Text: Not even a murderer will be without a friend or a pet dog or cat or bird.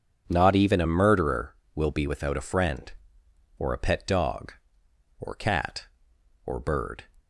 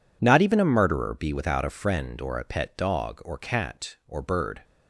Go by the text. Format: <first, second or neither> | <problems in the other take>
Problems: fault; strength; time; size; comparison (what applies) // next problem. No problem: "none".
first | skips "will"; at 1.1 s